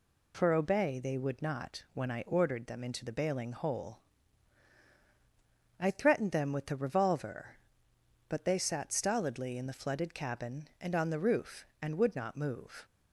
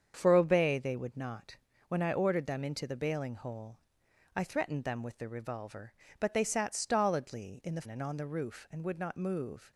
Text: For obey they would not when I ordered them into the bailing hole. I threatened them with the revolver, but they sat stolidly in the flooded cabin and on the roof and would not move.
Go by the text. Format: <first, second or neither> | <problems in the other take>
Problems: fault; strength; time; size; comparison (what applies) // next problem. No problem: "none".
first | starts louder than the rest; strong; until 1.1 s; 7.5 dB // pauses between "not" and "when"; slight; at 1.5 s; 0.32 s long // skips "flooded cabin"; at 7.8 s